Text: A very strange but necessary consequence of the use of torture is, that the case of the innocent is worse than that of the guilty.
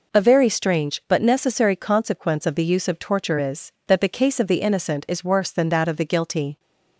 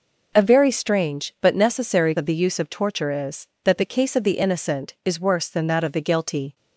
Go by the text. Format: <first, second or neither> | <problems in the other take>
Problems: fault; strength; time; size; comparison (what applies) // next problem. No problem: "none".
first | skips "consequence"; at 2.1 s